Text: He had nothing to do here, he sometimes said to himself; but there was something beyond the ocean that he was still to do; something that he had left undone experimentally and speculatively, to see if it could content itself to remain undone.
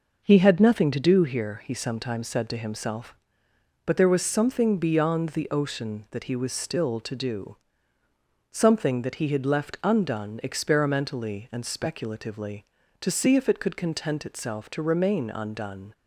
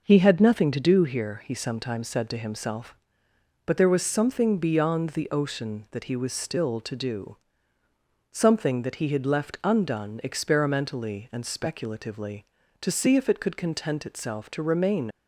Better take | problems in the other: first | stops before "undone"; at 15.1 s

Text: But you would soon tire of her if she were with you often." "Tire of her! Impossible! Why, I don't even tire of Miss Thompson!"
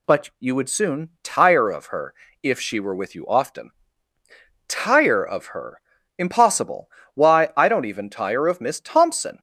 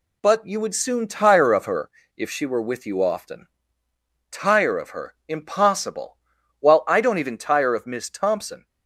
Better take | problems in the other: first | pauses between "her" and "if"; slight; at 1.8 s; 0.26 s long; slight in the first // says "While" for "Why"; at 6.5 s

